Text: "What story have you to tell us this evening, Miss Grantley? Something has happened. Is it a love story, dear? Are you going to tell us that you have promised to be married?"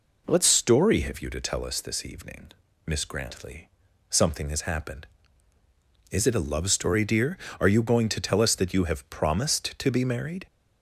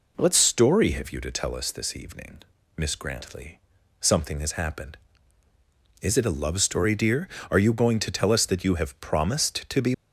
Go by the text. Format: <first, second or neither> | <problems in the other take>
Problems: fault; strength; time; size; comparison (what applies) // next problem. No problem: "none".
first | stops before "married"; at 9.9 s